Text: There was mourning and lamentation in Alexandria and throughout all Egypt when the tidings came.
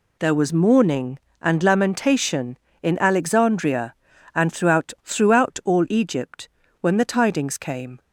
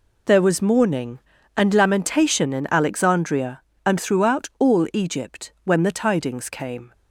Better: second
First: says "throughout" twice; at 5.0 s // pauses between "Egypt" and "when"; slight; at 6.4 s; 0.32 s long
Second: none

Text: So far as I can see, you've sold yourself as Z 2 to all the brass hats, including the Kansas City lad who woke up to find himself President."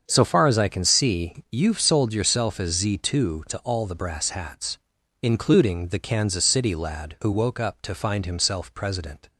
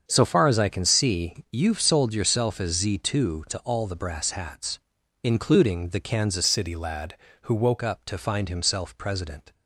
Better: first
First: starts louder than the rest; until 1.0 s; 7 dB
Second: starts louder than the rest; strong; until 1.0 s; 7 dB // changes voice from "City" to "woke"; from 6.4 to 7.7 s; 1.3 s long

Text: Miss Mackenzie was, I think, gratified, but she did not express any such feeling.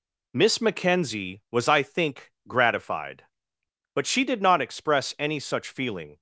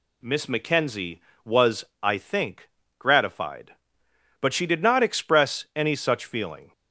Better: neither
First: none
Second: none

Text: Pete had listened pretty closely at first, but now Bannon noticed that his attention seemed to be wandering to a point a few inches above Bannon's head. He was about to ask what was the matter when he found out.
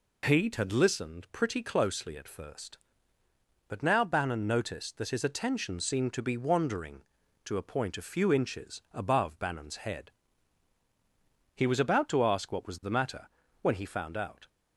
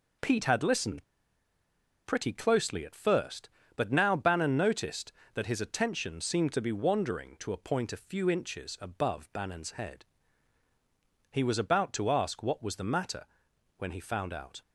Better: first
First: pauses between "matter" and "when"; slight; at 13.2 s; 0.34 s long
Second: pauses between "listened" and "pretty"; at 1.0 s; 1.0 s long // pauses between "matter" and "when"; noticeable; at 13.2 s; 0.52 s long

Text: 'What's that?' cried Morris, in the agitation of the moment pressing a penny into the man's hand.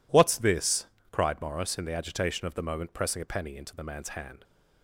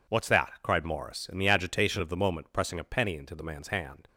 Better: second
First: says "this" for "that"; at 0.3 s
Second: none

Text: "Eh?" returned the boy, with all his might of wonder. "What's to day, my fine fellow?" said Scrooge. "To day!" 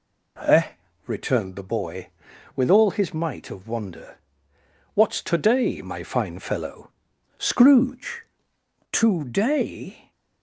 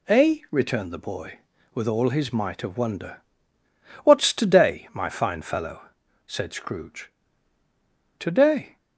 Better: second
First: skips "said"; at 7.1 s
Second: none

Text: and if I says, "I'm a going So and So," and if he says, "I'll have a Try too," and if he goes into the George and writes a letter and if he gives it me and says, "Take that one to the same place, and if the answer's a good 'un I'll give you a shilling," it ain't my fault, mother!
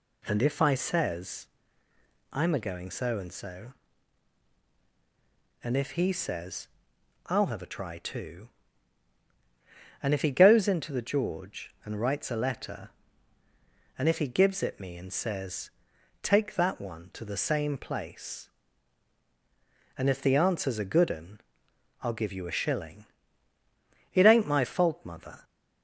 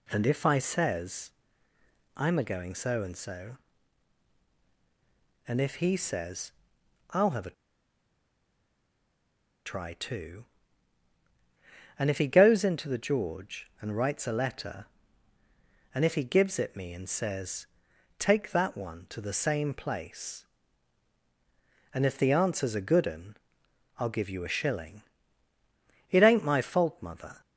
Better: first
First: pauses between "un" and "I'll"; noticeable; at 21.3 s; 0.62 s long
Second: pauses between "a" and "Try"; strong; at 7.5 s; 2.1 s long // pauses between "un" and "I'll"; noticeable; at 23.3 s; 0.62 s long

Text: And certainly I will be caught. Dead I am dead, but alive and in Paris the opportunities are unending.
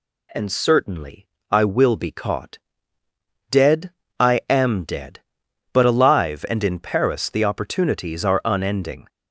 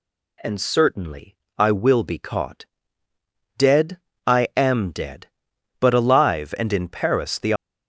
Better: first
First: pauses between "certainly" and "I"; slight; at 1.2 s; 0.24 s long // pauses between "Dead" and "I"; slight; at 3.8 s; 0.28 s long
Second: pauses between "certainly" and "I"; slight; at 1.3 s; 0.22 s long // pauses between "Dead" and "I"; slight; at 3.9 s; 0.28 s long // stops before "opportunities are unending"; at 7.5 s

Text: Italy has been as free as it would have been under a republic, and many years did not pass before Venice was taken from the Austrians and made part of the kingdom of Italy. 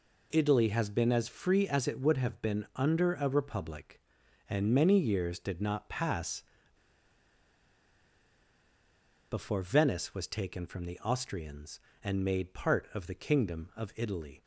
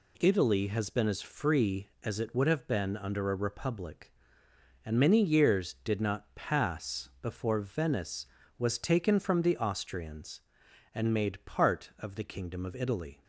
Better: second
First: pauses between "pass" and "before"; strong; at 6.4 s; 2.8 s long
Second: none

